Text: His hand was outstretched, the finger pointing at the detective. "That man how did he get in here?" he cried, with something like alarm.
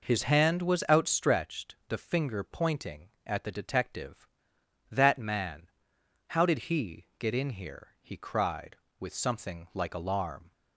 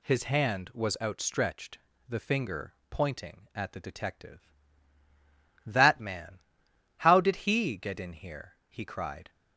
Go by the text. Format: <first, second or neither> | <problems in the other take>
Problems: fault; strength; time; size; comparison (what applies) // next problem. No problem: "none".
first | pauses between "finger" and "pointing"; slight; at 2.7 s; 0.16 s long // pauses between "man" and "how"; noticeable; at 6.3 s; 0.58 s long; noticeable in the first // stops before "with something like alarm"; at 9.2 s